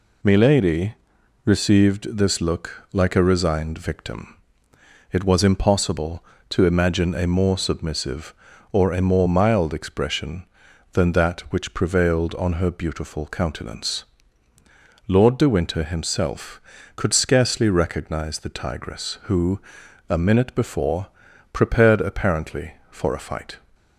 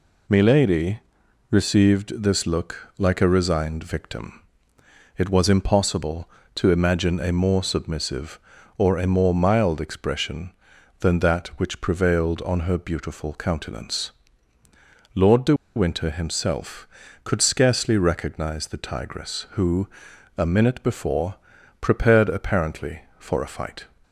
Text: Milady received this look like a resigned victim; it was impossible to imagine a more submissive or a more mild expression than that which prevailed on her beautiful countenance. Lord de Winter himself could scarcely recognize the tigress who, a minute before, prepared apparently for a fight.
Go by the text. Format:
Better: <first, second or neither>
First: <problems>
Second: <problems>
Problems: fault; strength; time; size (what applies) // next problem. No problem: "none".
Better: first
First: pauses between "Milady" and "received"; noticeable; at 0.9 s; 0.50 s long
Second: pauses between "Milady" and "received"; noticeable; at 0.9 s; 0.50 s long // pauses between "de" and "Winter"; slight; at 15.5 s; 0.22 s long